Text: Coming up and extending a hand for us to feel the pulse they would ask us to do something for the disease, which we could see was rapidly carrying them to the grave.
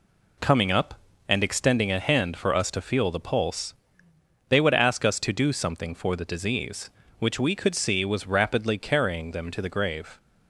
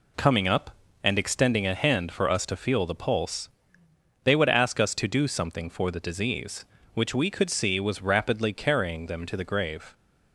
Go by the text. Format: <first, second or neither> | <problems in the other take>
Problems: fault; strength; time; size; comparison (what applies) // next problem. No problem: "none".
neither | pauses between "pulse" and "they"; noticeable; the same in both